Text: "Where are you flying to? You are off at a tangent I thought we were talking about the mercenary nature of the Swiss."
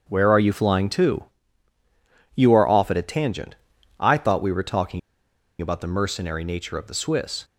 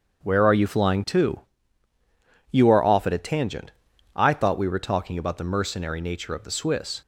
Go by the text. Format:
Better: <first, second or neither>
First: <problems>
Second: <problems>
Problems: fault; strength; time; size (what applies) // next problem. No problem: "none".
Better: second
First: starts louder than the rest; strong; until 1.1 s; 7 dB // pauses between "tangent" and "I"; at 3.5 s; 0.44 s long // pauses between "talking" and "about"; noticeable; at 4.9 s; 0.60 s long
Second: starts louder than the rest; strong; until 1.2 s; 7 dB // pauses between "tangent" and "I"; at 3.7 s; 0.44 s long